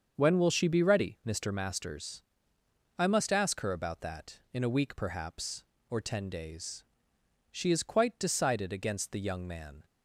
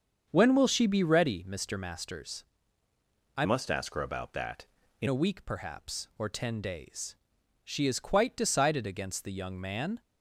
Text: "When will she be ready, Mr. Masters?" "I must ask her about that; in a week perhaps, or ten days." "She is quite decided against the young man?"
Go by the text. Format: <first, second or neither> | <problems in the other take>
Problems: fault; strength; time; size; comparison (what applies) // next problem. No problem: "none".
first | starts louder than the rest; until 1.3 s; 7 dB; also in the first // changes voice from "must" to "in"; from 3.4 to 5.0 s; 1.6 s long